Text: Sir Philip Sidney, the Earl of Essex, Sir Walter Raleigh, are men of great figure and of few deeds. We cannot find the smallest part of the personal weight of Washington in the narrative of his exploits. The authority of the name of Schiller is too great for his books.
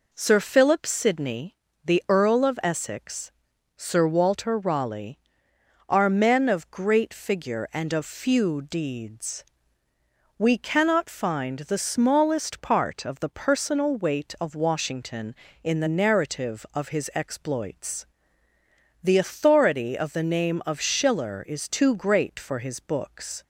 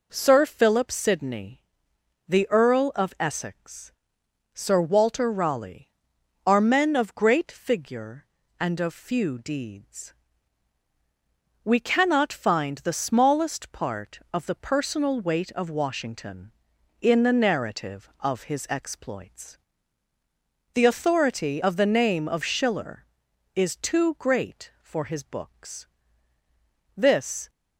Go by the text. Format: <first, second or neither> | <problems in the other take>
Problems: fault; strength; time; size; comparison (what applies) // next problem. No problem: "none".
first | goes on to say "This"; from 26.9 s on; 0.54 s long